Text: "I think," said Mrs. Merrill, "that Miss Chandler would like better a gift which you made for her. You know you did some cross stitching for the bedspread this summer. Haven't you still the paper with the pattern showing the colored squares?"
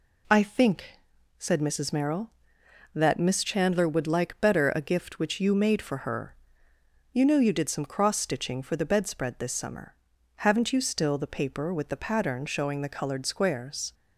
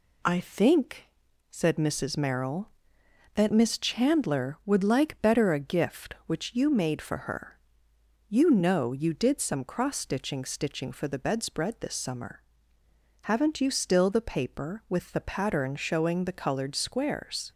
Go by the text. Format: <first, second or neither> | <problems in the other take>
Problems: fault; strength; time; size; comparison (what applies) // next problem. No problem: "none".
first | says "stitching" twice; at 10.4 s